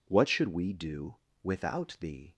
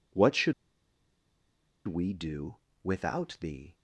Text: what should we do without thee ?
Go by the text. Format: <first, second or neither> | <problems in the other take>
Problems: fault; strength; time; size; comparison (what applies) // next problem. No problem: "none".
first | pauses between "should" and "we"; strong; at 0.5 s; 1.3 s long // pauses between "do" and "without"; slight; at 2.5 s; 0.28 s long; slight in the first